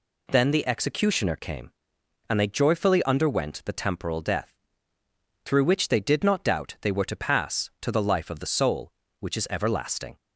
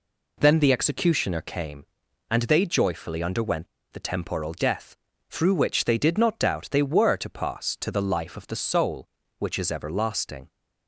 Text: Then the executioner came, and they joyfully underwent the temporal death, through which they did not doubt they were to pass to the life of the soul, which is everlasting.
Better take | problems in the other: first | pauses between "underwent" and "the"; slight; at 3.6 s; 0.26 s long

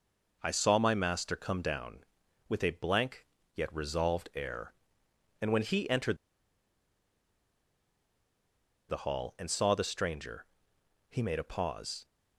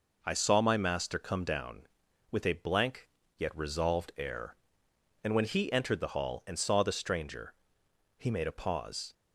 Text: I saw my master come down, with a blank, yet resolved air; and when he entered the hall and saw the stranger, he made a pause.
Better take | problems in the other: second | pauses between "entered" and "the"; strong; at 6.1 s; 2.7 s long

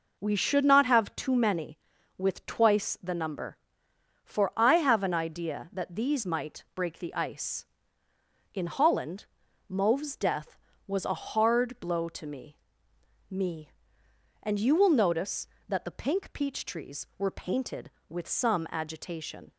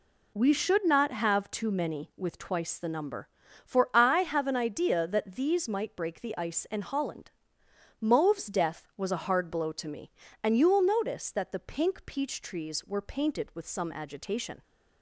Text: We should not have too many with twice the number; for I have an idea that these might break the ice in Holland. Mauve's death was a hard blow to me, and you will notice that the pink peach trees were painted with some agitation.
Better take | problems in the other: second | says "me" twice; at 13.2 s

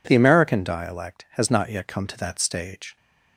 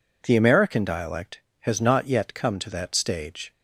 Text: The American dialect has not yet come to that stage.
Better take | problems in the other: neither | none

